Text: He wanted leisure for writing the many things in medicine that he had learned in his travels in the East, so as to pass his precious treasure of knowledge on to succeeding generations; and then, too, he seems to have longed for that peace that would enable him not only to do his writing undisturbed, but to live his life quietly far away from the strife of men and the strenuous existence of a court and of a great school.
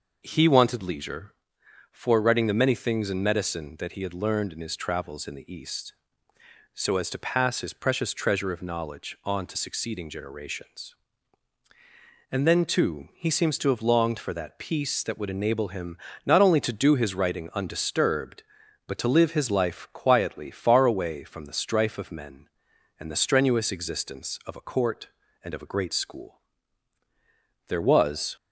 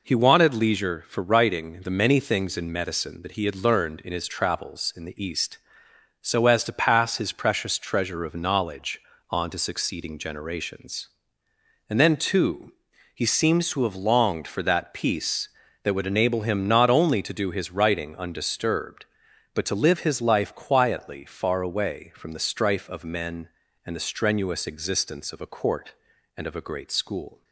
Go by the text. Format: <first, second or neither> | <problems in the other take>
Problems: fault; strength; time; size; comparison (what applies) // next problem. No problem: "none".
second | pauses between "him" and "not"; slight; at 15.9 s; 0.30 s long // goes on to say "There was"; noticeable; from 27.6 s on; 0.66 s long